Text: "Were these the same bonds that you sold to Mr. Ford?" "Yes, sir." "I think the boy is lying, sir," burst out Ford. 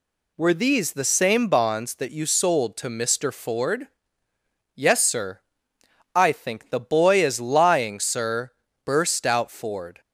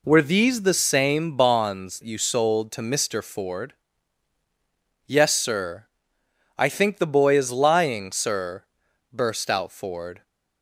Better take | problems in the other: first | skips "that"; at 2.0 s

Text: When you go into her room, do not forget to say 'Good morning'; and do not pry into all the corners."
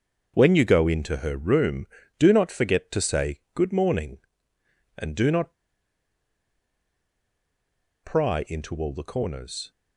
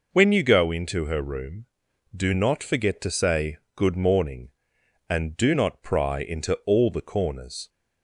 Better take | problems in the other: second | starts louder than the rest; until 1.3 s; 6.5 dB // pauses between "say" and "Good"; slight; at 3.3 s; 0.16 s long; slight in the second // pauses between "not" and "pry"; strong; at 5.5 s; 2.4 s long

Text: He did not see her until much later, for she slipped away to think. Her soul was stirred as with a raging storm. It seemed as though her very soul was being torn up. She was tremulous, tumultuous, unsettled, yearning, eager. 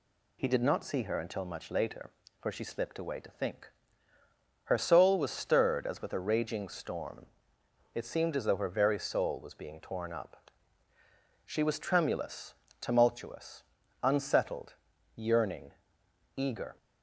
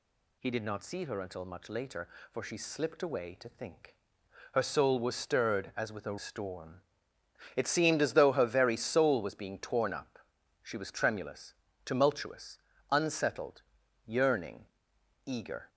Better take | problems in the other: first | skips "raging"; at 6.1 s

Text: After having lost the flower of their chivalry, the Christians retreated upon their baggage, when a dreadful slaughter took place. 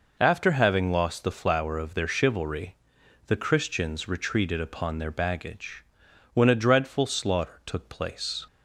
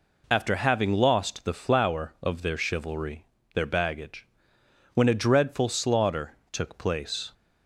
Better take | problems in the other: first | skips "the Christians retreated upon"; at 3.3 s // pauses between "slaughter" and "took"; slight; at 6.3 s; 0.16 s long

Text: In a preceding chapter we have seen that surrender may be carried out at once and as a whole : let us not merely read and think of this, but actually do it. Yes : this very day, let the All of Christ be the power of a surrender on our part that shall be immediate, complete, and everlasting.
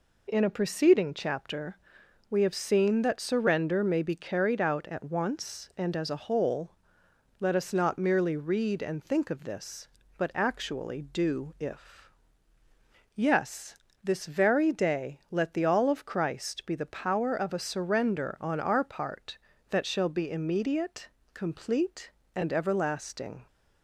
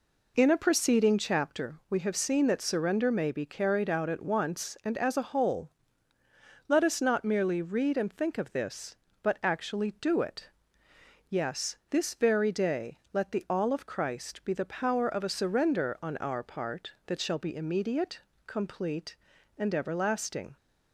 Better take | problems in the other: second | pauses between "chapter" and "we"; noticeable; at 1.7 s; 0.50 s long // says "if" for "it"; at 11.5 s

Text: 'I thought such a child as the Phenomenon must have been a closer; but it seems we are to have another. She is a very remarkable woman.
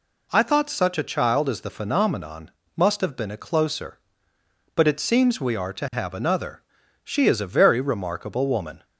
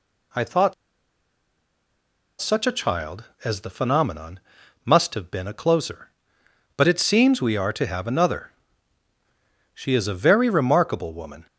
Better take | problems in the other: first | pauses between "thought" and "such"; strong; at 0.7 s; 1.6 s long // pauses between "Phenomenon" and "must"; at 4.3 s; 0.44 s long; slight in the first

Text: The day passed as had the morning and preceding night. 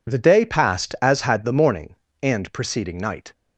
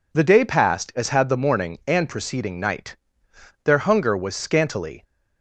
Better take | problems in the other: first | goes on to say "Their hunger was scantily"; from 3.6 s on; 1.3 s long

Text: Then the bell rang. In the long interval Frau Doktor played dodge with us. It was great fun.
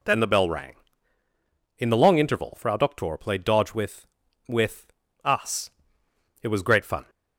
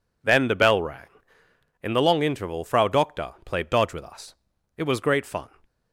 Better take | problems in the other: second | says "with" twice; at 4.4 s

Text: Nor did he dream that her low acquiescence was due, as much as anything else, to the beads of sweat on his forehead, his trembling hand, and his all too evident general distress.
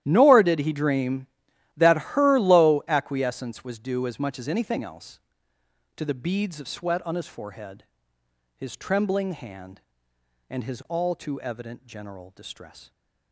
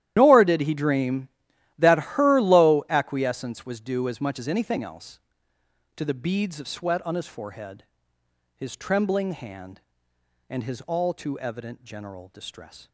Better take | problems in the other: first | loses the start of "Nor"; at 0.1 s; 100 ms // starts louder than the rest; strong; until 1.1 s; 12.5 dB; strong in the first

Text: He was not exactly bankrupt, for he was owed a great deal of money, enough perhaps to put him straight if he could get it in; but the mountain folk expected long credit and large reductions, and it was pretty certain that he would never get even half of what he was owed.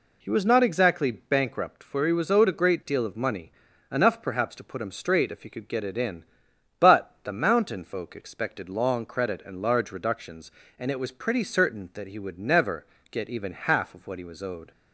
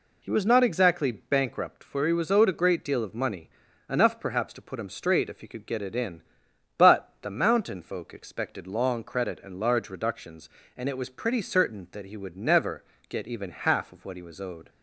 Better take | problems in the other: neither | pauses between "never" and "get"; slight; the same in both

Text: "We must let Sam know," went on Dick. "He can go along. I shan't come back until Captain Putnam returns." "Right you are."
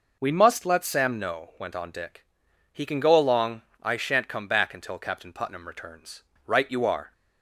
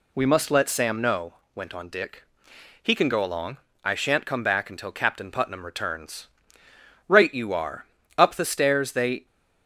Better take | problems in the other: first | goes on to say "Up the stairs they"; noticeable; from 8.1 s on; 1.0 s long

